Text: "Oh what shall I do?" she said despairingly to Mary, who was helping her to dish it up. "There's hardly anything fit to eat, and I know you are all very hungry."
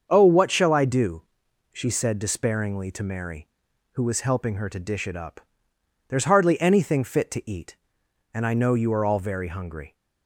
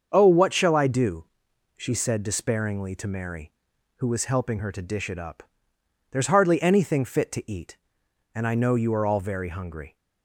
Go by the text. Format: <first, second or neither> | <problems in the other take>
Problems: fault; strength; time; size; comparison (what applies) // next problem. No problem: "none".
neither | starts louder than the rest; the same in both